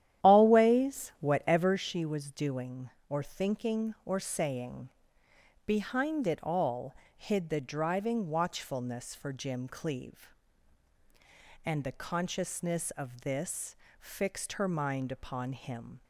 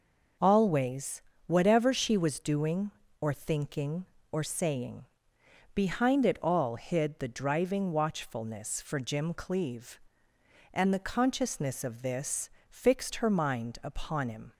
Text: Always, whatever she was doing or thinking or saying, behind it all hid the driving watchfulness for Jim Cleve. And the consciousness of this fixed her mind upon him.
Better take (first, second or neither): second